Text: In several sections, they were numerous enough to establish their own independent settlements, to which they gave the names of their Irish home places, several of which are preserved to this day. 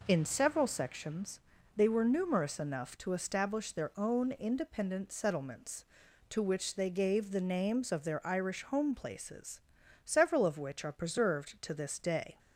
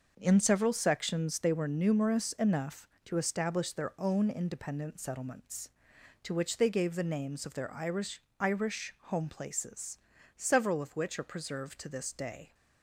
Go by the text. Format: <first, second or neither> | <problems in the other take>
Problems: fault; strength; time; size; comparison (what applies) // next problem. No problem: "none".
first | says "Irish" twice; at 8.3 s